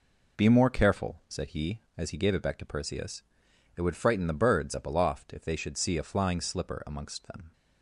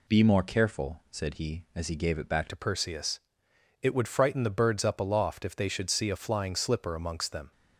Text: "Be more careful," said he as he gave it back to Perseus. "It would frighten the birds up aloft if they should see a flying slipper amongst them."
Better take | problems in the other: first | changes voice at "to"; from 2.4 s on; 5.1 s long

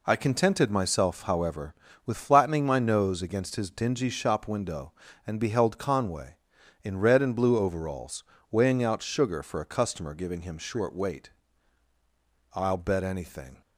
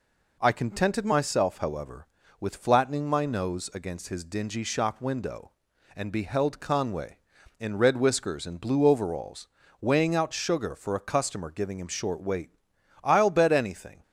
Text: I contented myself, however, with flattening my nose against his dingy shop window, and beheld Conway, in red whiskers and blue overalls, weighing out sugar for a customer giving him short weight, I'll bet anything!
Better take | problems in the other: second | skips "whiskers"; at 7.2 s

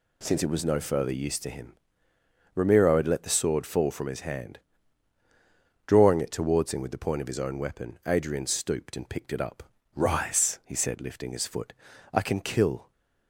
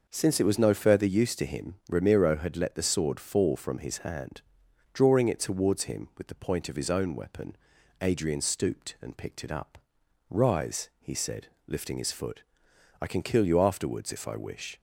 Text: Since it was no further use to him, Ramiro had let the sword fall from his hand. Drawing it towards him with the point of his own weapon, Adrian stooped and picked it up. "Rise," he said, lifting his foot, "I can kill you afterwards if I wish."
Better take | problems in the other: second | stops before "you afterwards if I wish"; at 12.9 s

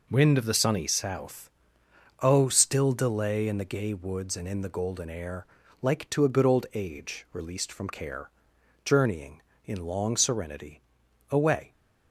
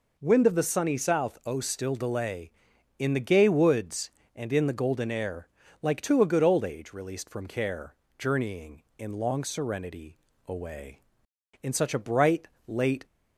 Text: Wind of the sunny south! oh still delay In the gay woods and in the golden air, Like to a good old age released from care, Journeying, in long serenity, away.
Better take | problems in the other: first | goes on to say "In such a bright late"; from 11.6 s on; 1.4 s long

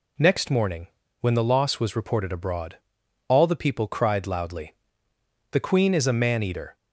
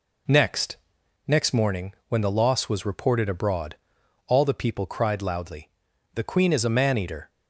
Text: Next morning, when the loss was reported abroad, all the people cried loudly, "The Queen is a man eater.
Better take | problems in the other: first | says "Next" twice; at 1.2 s

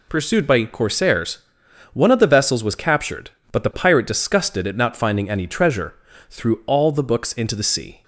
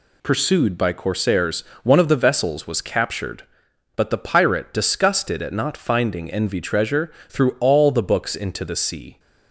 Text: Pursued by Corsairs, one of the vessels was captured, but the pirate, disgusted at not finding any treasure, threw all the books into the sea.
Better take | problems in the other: first | says "envy" for "any"; at 6.2 s

